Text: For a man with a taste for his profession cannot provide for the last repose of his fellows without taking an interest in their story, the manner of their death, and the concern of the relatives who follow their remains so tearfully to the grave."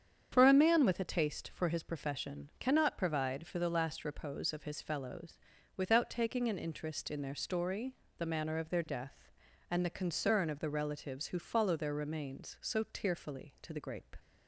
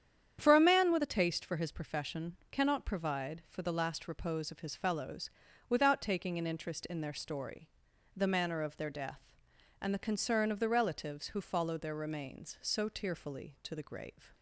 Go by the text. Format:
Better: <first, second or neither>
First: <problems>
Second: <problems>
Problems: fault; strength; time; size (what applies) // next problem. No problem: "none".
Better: second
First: starts louder than the rest; strong; until 1.3 s; 8 dB // pauses between "fellows" and "without"; at 5.3 s; 0.40 s long // says "grape" for "grave"; at 13.7 s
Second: starts louder than the rest; strong; until 1.4 s; 9 dB // pauses between "fellows" and "without"; slight; at 5.3 s; 0.36 s long